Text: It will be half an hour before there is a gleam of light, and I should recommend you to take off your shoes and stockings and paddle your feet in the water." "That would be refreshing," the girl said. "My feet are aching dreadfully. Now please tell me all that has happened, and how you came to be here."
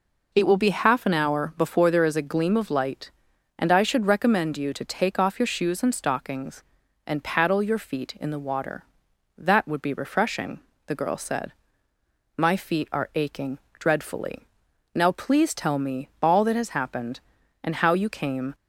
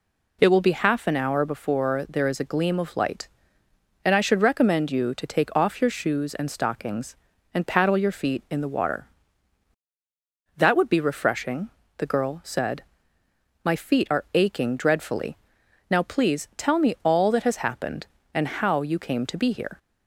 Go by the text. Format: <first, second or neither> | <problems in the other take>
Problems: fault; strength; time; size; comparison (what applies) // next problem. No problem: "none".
second | pauses between "aching" and "dreadfully"; slight; at 13.5 s; 0.18 s long // pauses between "me" and "all"; slight; at 16.0 s; 0.16 s long // stops before "to be here"; at 18.5 s